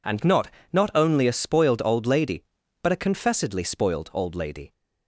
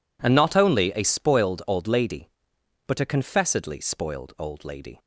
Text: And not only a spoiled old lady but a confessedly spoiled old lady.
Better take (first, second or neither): second